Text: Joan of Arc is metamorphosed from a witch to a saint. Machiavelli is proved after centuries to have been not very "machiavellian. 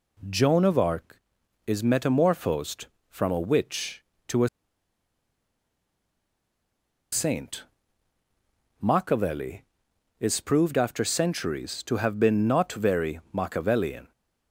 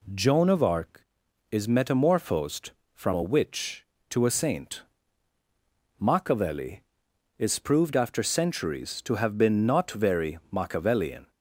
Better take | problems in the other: second | pauses between "a" and "saint"; strong; at 4.4 s; 2.6 s long

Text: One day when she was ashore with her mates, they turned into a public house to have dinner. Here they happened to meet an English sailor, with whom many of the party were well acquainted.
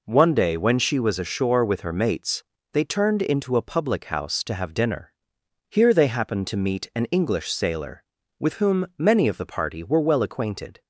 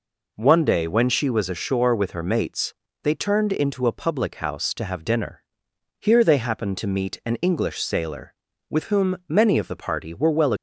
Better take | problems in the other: first | stops before "acquainted"; at 10.5 s

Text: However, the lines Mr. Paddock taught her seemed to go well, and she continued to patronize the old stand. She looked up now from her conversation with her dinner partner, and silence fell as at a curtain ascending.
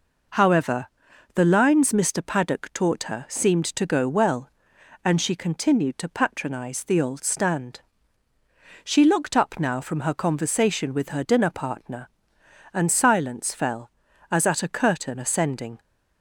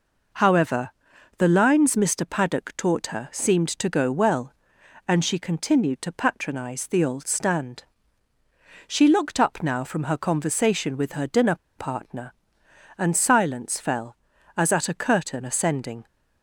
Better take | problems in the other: first | pauses between "dinner" and "partner"; slight; at 11.5 s; 0.21 s long

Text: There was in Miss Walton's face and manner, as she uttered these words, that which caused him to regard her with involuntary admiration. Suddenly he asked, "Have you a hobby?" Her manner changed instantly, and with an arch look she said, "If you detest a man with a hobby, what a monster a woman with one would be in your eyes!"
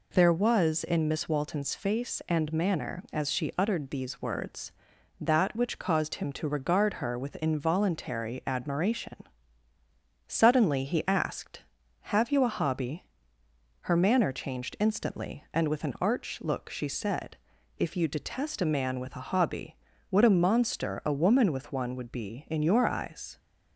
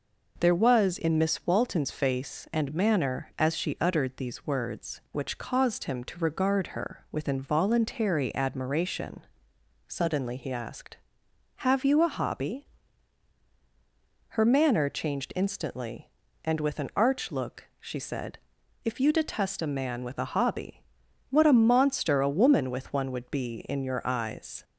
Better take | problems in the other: first | skips "that"; at 5.0 s

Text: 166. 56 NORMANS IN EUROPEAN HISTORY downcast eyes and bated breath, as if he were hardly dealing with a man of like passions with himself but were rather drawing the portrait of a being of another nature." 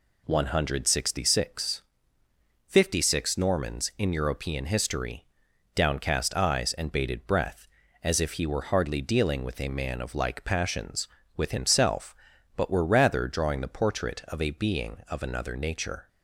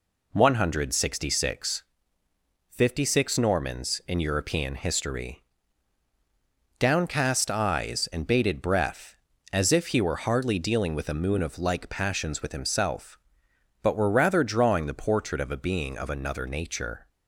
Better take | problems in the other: first | pauses between "HISTORY" and "downcast"; strong; at 5.4 s; 1.3 s long; noticeable in the first // says "moon" for "man"; at 11.1 s

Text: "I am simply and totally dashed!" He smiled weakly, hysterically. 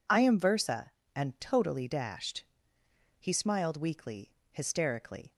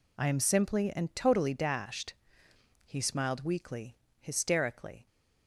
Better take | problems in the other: second | says "versa" for "simply"; at 0.3 s

